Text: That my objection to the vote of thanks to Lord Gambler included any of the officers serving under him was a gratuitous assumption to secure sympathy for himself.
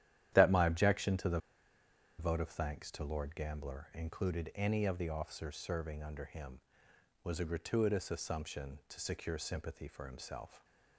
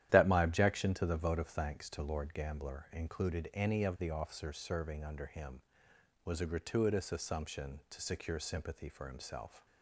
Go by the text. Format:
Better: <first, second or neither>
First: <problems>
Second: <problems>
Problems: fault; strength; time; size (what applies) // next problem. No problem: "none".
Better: second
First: starts louder than the rest; strong; until 1.3 s; 11.5 dB // pauses between "the" and "vote"; noticeable; at 1.3 s; 0.81 s long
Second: starts louder than the rest; strong; until 1.1 s; 11.5 dB